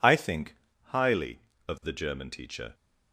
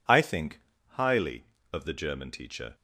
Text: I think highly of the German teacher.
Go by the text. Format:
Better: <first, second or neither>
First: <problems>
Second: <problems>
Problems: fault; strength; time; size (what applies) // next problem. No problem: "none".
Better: neither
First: pauses between "think" and "highly"; slight; at 0.5 s; 0.30 s long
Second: pauses between "think" and "highly"; slight; at 0.5 s; 0.30 s long